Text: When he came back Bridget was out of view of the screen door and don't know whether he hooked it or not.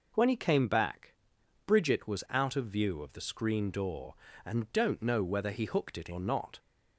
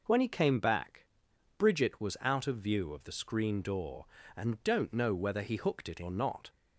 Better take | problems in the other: neither | pauses between "back" and "Bridget"; noticeable; the same in both

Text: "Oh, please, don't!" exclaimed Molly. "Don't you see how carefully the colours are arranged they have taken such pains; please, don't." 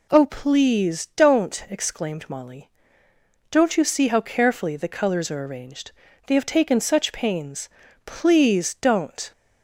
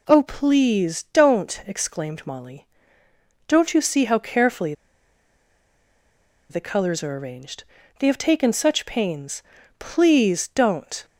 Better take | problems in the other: first | pauses between "carefully" and "the"; strong; at 4.7 s; 1.7 s long // pauses between "arranged" and "they"; slight; at 7.6 s; 0.34 s long; slight in the first

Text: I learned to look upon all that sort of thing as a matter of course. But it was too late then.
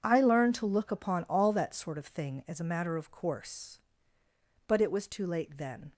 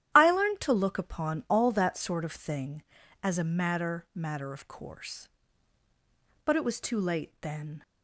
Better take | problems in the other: first | starts louder than the rest; strong; until 1.1 s; 11.5 dB // says "matter" twice; at 4.1 s

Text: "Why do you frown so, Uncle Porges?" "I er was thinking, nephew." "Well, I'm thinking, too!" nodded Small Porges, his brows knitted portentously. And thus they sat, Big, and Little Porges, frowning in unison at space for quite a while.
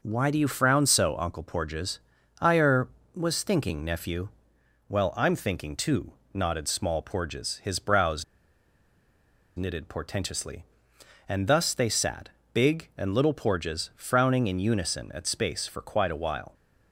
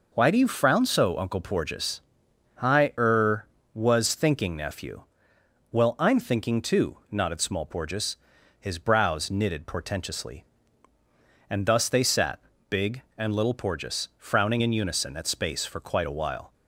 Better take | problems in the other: second | pauses between "brows" and "knitted"; strong; at 8.2 s; 1.3 s long

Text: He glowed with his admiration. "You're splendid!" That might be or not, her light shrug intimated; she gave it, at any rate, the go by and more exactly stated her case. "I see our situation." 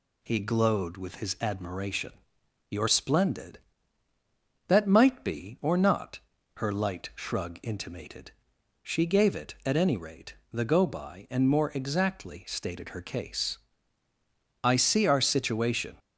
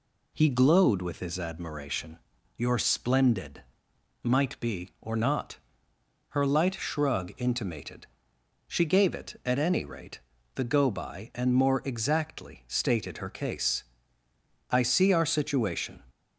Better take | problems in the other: first | skips "That"; at 3.9 s

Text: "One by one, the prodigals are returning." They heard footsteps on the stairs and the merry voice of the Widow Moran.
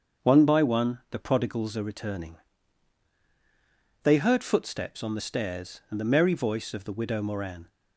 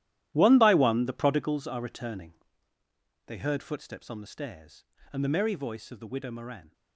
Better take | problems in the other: first | gets quieter; strong; throughout; 14.5 dB // starts louder than the rest; strong; until 1.3 s; 13 dB; also in the first

